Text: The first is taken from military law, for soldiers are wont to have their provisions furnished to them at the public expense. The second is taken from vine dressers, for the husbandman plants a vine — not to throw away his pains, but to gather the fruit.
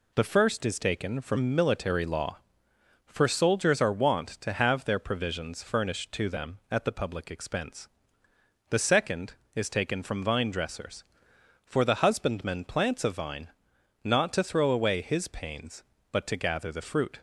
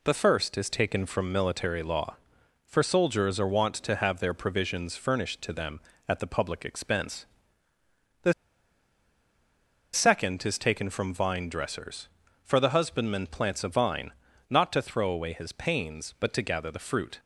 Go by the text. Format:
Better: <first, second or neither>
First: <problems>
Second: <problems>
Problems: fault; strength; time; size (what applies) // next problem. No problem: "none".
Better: first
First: none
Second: pauses between "The" and "second"; strong; at 8.3 s; 1.5 s long